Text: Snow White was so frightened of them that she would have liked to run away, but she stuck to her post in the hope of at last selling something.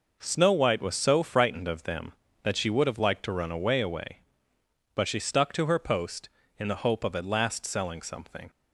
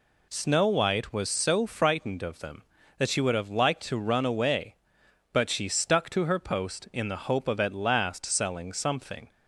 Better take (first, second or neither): second